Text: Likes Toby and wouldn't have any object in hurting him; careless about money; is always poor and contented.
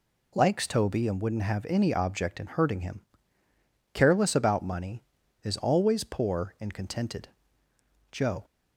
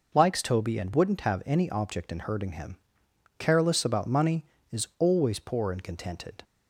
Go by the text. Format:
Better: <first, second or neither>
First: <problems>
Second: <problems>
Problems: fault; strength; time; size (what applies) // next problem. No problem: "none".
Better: second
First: goes on to say "Joe"; slight; from 8.1 s on; 0.34 s long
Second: none